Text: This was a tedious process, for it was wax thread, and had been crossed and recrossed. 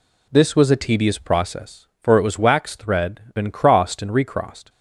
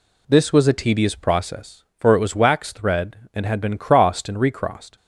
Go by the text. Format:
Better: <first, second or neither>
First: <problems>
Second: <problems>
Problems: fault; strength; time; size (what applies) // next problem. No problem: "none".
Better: second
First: skips "and had"; at 3.2 s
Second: none